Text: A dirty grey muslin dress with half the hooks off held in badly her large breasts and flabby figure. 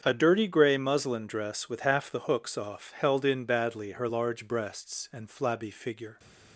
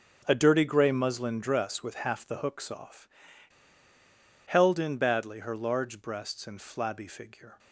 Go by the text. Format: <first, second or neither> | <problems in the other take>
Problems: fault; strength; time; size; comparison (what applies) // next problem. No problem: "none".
first | starts louder than the rest; until 1.2 s; 6.5 dB; strong in the first // pauses between "off" and "held"; strong; at 3.0 s; 1.3 s long